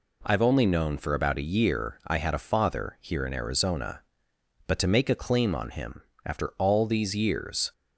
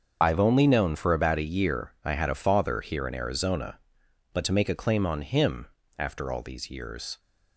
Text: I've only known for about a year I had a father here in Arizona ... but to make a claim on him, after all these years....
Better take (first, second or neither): first